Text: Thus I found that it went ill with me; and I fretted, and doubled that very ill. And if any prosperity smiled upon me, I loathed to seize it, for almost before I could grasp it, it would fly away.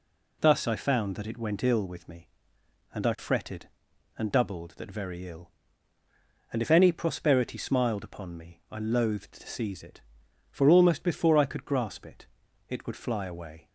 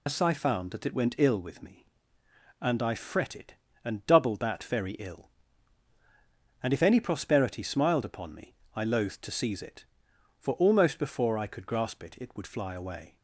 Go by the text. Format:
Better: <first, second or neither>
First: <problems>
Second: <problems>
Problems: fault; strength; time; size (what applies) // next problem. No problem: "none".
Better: first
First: none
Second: loses the start of "Thus"; at 0.0 s; 105 ms